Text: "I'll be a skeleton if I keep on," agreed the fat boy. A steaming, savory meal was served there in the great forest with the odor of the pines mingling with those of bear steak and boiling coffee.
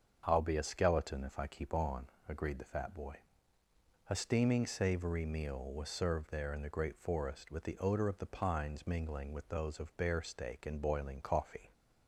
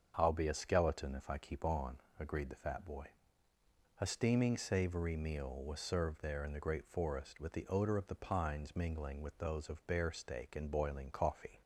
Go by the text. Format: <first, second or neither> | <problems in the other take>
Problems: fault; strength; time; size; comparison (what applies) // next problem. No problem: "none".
neither | starts louder than the rest; the same in both